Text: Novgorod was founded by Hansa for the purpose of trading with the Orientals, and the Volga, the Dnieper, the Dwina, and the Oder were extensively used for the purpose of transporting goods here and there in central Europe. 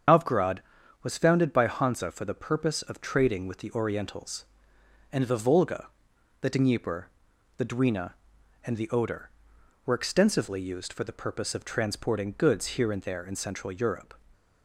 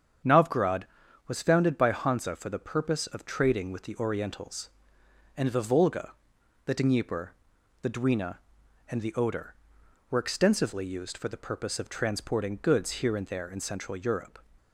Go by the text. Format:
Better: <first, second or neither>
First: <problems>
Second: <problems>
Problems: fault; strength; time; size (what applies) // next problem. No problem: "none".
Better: second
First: loses the start of "Novgorod"; at 0.0 s; 80 ms // starts louder than the rest; strong; until 1.5 s; 7.5 dB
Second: starts louder than the rest; strong; until 1.6 s; 8 dB